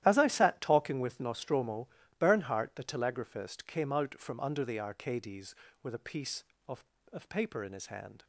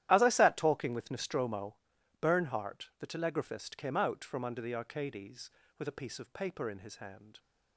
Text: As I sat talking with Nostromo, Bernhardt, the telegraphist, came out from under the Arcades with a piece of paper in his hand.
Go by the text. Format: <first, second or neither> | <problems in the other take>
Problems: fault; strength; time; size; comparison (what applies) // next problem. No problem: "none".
second | starts louder than the rest; strong; until 1.0 s; 12.5 dB; strong in the second // says "of" twice; at 7.1 s